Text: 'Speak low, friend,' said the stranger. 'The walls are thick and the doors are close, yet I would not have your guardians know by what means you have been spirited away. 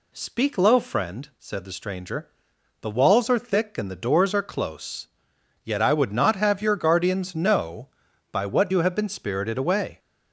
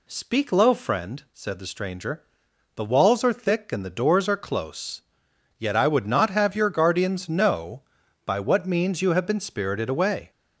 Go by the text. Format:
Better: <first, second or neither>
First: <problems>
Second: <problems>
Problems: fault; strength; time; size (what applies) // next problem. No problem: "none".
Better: second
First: skips "means"; at 8.7 s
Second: none